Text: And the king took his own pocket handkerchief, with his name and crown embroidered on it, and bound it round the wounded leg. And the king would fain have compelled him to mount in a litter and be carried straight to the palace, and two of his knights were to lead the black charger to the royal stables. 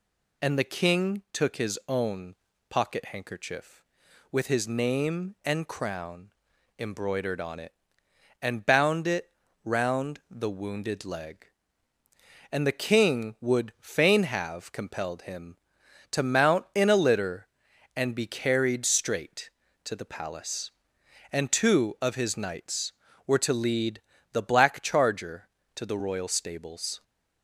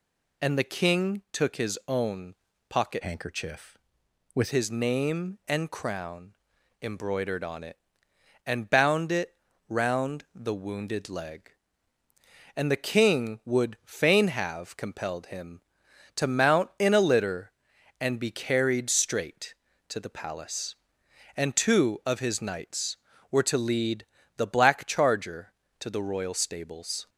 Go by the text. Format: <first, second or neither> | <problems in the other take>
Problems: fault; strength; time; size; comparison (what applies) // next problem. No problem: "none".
first | pauses between "own" and "pocket"; slight; at 2.3 s; 0.34 s long; slight in the first // changes voice from "handkerchief" to "with"; from 3.0 to 4.5 s; 1.5 s long // pauses between "crown" and "embroidered"; noticeable; at 6.3 s; 0.48 s long; noticeable in the first // pauses between "it" and "round"; slight; at 9.3 s; 0.34 s long; slight in the first // pauses between "lead" and "the"; slight; at 24.0 s; 0.32 s long; slight in the first